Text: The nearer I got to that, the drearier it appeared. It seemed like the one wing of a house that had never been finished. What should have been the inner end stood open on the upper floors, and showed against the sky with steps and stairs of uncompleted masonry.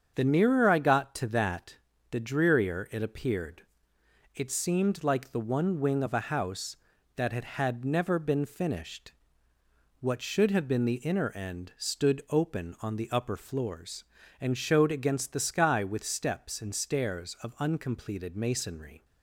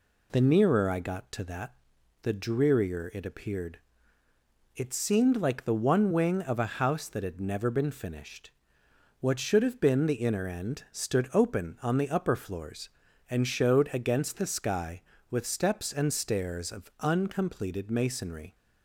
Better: second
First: starts louder than the rest; strong; until 1.1 s; 7 dB // says "had" twice; at 7.4 s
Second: none

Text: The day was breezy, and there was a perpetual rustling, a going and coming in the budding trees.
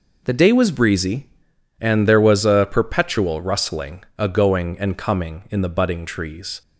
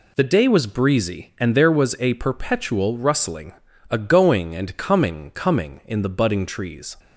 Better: first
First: none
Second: says "coming" twice; at 5.3 s

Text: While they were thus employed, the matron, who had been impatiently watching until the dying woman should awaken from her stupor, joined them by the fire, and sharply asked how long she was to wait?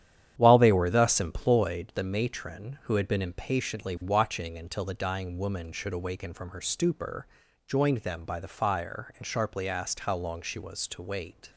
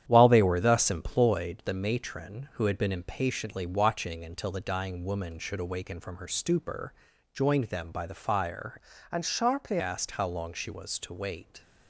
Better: first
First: starts louder than the rest; strong; until 1.3 s; 10 dB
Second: starts louder than the rest; strong; until 1.0 s; 10 dB // changes voice from "and" to "sharply"; from 9.1 to 9.7 s; 0.6 s long

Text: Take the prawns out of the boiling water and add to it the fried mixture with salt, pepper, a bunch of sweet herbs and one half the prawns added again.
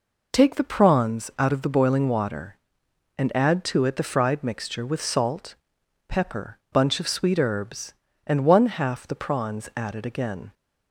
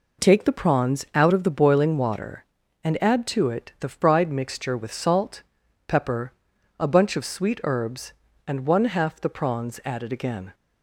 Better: second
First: skips "a"; at 6.6 s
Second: none

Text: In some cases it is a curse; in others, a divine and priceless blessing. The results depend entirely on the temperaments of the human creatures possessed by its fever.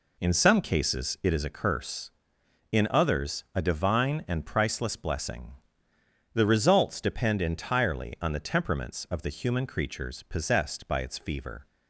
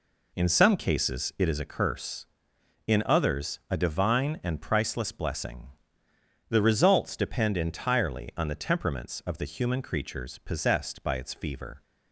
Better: neither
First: none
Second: none

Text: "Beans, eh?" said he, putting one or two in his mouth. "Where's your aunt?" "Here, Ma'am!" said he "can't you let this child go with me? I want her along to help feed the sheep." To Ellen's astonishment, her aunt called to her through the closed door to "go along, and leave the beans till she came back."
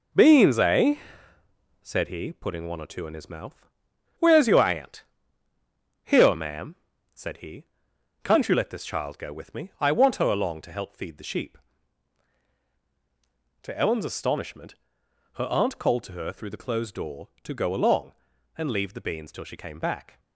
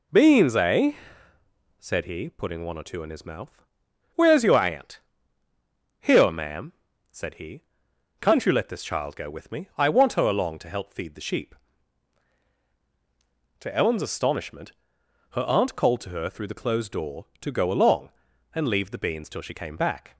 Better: second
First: gets quieter; noticeable; throughout; 6 dB // pauses between "he" and "can't"; noticeable; at 7.6 s; 0.60 s long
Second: pauses between "he" and "can't"; noticeable; at 7.6 s; 0.60 s long

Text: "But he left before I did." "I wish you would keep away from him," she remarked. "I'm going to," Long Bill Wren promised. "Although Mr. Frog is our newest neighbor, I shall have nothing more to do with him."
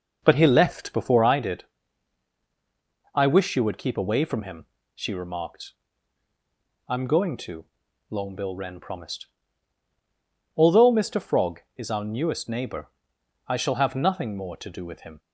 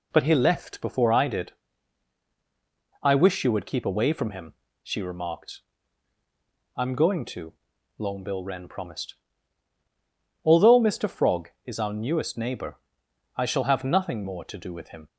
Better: second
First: starts louder than the rest; noticeable; until 1.4 s; 5.5 dB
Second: none

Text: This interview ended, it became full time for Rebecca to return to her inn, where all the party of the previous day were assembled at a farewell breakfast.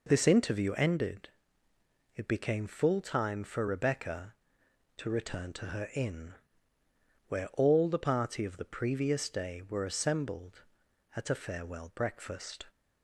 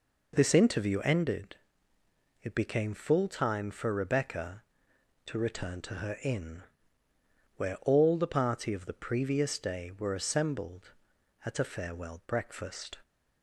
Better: neither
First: none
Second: none

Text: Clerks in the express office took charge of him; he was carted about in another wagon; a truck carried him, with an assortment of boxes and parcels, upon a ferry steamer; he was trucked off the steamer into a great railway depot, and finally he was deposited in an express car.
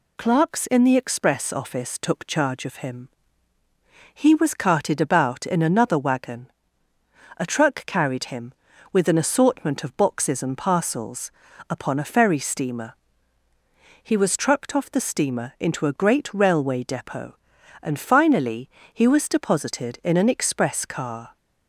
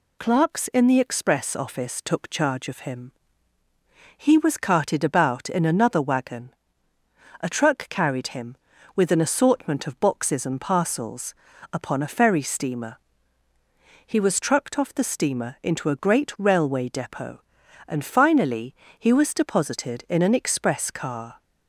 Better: neither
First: pauses between "finally" and "he"; slight; at 18.6 s; 0.24 s long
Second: pauses between "finally" and "he"; slight; at 18.7 s; 0.24 s long

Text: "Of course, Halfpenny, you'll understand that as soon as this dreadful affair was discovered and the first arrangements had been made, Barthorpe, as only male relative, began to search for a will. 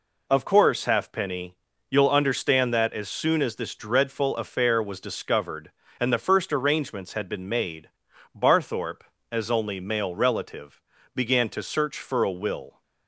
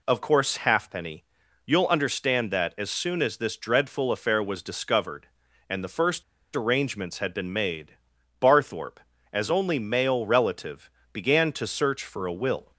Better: first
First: none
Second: pauses between "first" and "arrangements"; slight; at 6.2 s; 0.32 s long

